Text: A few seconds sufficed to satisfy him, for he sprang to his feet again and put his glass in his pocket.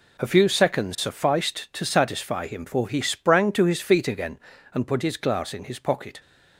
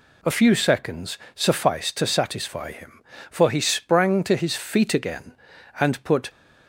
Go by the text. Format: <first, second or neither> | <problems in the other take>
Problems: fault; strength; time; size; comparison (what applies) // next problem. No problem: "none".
first | pauses between "seconds" and "sufficed"; slight; at 1.1 s; 0.18 s long // stops before "his glass in his pocket"; at 6.2 s